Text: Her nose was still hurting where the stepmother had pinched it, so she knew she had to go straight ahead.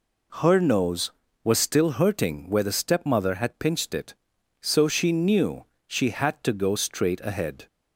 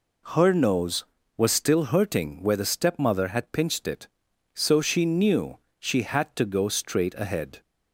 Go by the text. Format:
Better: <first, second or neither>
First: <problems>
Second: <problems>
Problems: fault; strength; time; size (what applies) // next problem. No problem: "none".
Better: neither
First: pauses between "knew" and "she"; slight; at 5.6 s; 0.24 s long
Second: pauses between "knew" and "she"; slight; at 5.5 s; 0.23 s long